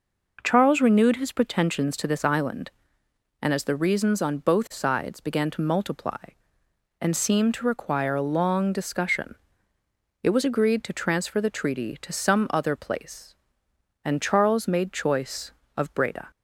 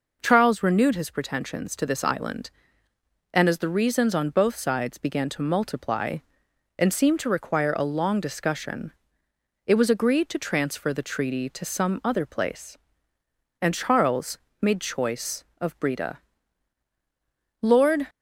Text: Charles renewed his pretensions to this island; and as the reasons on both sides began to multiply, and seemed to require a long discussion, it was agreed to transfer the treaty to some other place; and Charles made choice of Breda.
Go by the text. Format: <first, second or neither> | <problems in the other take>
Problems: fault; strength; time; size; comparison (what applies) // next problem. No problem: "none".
first | pauses between "Charles" and "made"; slight; at 14.3 s; 0.24 s long // goes on to say "Lord"; slight; from 17.6 s on; 0.46 s long